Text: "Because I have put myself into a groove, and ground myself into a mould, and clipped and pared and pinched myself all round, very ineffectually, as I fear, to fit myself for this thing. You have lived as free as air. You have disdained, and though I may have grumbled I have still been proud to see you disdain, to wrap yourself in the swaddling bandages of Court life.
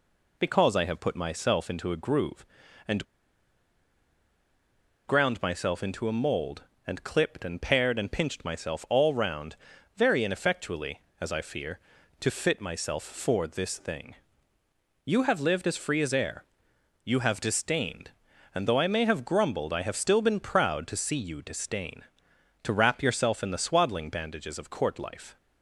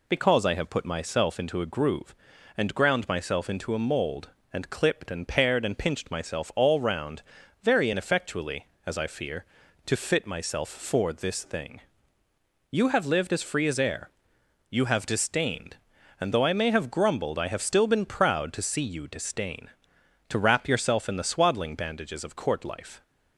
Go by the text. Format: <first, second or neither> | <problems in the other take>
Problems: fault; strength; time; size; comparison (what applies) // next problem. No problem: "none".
second | pauses between "and" and "ground"; strong; at 3.0 s; 2.0 s long